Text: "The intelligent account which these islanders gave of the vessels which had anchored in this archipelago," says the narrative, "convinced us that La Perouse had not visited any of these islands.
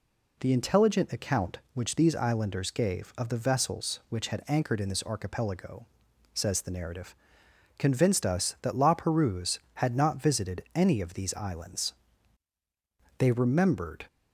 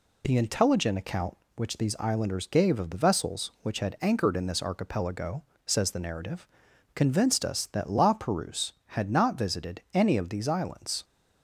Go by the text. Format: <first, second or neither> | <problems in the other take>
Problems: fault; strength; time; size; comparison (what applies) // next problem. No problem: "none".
second | goes on to say "They remembered"; noticeable; from 13.1 s on; 0.88 s long